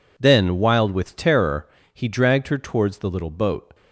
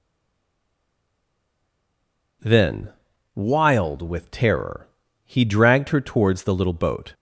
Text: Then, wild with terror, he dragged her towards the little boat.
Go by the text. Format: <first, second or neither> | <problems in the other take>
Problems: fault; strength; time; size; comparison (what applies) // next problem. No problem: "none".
first | stays silent before the first word; until 2.4 s; 2.4 s long